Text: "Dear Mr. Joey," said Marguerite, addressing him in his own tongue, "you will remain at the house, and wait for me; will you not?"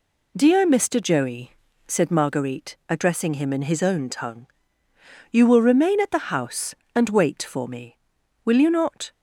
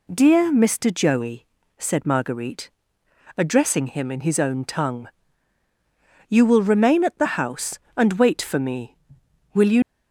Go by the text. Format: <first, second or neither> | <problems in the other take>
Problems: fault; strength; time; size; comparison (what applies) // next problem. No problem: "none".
first | stops before "not"; at 9.8 s